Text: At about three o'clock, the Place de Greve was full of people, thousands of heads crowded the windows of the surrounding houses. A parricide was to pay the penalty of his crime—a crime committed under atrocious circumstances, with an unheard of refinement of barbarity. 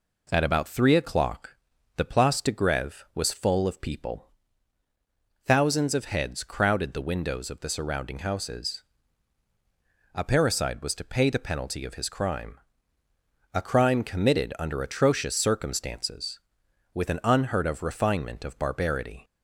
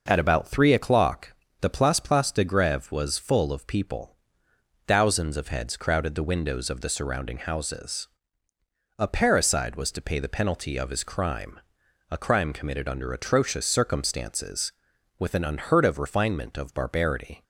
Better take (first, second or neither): first